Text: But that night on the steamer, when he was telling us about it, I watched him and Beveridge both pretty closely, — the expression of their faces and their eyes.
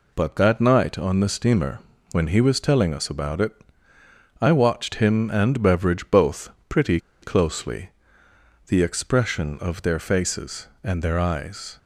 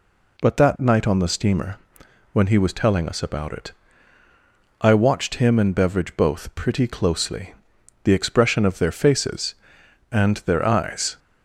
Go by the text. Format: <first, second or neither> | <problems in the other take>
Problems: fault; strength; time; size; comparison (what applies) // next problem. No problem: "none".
second | pauses between "both" and "pretty"; slight; at 6.5 s; 0.18 s long // pauses between "pretty" and "closely"; slight; at 6.9 s; 0.23 s long